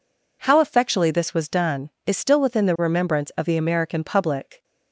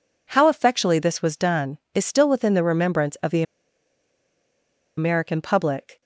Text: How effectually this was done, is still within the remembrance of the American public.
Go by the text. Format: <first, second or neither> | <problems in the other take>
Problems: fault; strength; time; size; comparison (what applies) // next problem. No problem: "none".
first | pauses between "the" and "American"; strong; at 3.4 s; 1.5 s long